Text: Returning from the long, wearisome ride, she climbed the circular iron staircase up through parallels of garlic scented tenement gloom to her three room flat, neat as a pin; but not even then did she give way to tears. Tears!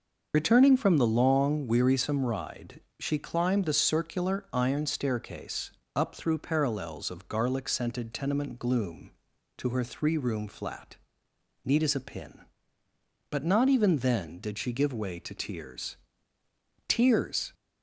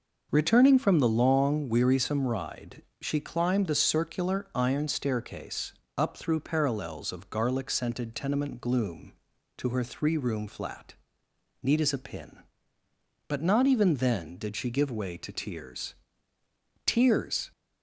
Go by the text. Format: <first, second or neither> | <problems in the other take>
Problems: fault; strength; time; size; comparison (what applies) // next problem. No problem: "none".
second | loses the start of "Returning"; at 0.3 s; 50 ms // starts louder than the rest; noticeable; until 1.3 s; 6 dB // pauses between "staircase" and "up"; slight; at 5.7 s; 0.24 s long; slight in the second